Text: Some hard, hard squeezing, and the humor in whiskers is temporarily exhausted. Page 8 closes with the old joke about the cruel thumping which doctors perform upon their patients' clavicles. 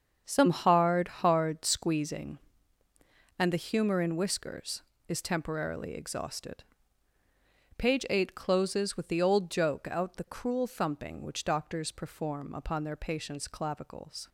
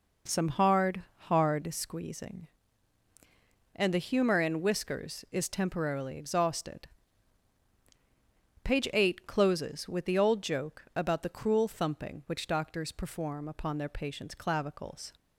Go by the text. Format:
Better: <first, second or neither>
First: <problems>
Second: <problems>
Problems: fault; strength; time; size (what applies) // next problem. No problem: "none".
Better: second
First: starts louder than the rest; until 1.2 s; 7 dB // says "out" for "about"; at 9.9 s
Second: none